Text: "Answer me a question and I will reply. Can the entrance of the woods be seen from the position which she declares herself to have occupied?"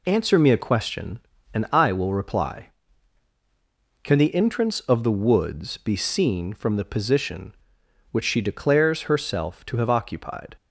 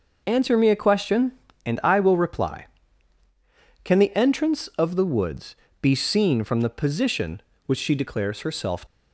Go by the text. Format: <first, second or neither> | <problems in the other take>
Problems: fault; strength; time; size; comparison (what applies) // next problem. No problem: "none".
first | pauses between "woods" and "be"; slight; at 5.5 s; 0.26 s long // stops before "to have occupied"; at 8.8 s